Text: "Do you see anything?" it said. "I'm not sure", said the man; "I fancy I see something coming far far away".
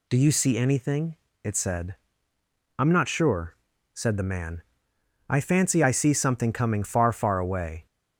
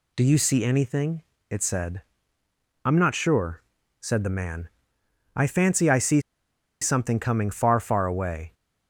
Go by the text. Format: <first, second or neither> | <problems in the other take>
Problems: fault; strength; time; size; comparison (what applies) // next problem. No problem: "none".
first | pauses between "see" and "something"; noticeable; at 6.1 s; 0.61 s long